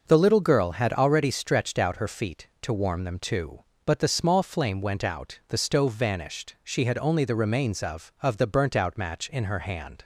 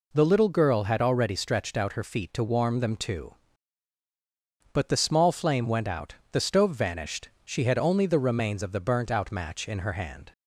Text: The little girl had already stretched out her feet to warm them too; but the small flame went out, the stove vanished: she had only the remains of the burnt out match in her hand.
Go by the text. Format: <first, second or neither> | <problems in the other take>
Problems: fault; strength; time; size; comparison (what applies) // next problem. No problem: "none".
second | says "of" twice; at 8.2 s